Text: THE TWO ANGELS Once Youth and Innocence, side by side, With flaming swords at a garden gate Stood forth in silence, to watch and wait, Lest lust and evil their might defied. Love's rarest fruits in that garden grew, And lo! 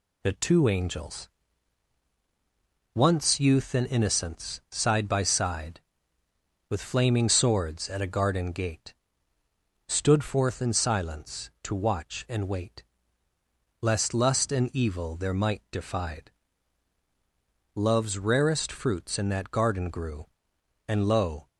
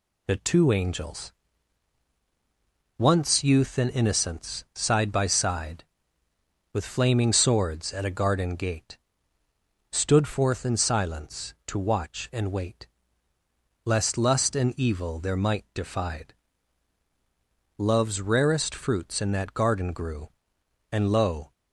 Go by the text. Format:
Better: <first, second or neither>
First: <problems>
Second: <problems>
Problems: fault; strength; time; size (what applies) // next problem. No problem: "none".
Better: neither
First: pauses between "ANGELS" and "Once"; strong; at 1.2 s; 1.6 s long // pauses between "gate" and "Stood"; noticeable; at 8.9 s; 0.94 s long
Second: pauses between "ANGELS" and "Once"; strong; at 1.3 s; 1.6 s long // pauses between "gate" and "Stood"; noticeable; at 8.9 s; 0.94 s long